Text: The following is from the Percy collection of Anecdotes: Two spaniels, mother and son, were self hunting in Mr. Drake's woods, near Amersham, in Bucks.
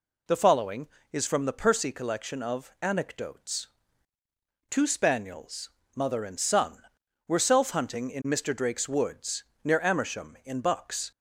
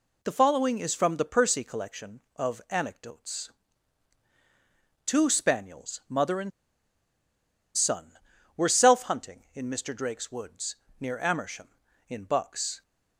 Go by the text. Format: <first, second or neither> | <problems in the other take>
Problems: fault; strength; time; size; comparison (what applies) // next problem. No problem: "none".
first | pauses between "and" and "son"; strong; at 6.5 s; 1.2 s long